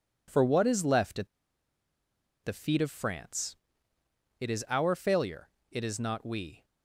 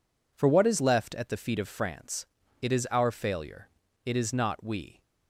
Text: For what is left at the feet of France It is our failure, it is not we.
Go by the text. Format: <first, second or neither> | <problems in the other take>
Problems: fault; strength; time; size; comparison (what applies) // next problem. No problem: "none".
second | pauses between "at" and "the"; at 1.2 s; 1.1 s long // pauses between "France" and "It"; noticeable; at 3.5 s; 0.86 s long; slight in the second